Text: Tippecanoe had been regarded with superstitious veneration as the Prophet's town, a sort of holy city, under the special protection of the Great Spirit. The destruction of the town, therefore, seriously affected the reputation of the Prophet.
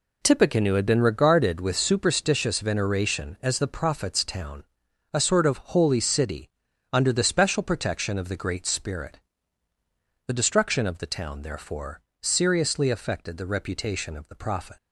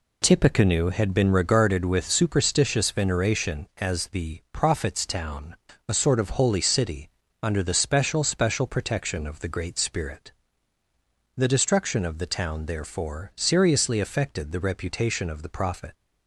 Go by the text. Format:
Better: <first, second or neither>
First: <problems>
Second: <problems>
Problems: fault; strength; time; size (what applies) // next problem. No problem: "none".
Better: first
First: none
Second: says "special" twice; at 8.2 s